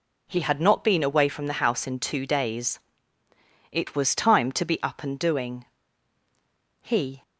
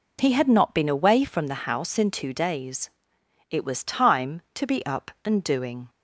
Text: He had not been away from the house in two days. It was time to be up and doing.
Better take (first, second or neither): second